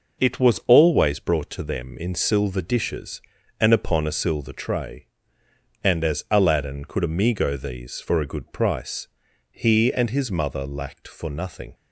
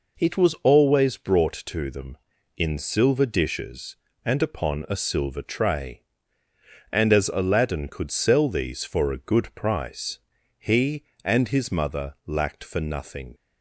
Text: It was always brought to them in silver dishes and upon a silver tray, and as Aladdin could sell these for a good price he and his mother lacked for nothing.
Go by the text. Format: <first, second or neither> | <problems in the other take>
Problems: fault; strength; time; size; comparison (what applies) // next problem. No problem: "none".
second | says "amigo" for "sell"; at 7.0 s // pauses between "price" and "he"; noticeable; at 9.0 s; 0.46 s long; also in the second